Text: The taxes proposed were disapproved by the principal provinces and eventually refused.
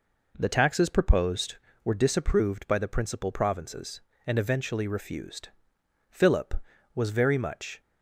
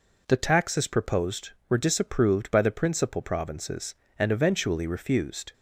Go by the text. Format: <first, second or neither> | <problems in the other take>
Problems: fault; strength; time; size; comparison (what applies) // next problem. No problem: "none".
second | goes on to say "Philip was very much"; strong; from 6.0 s on; 1.7 s long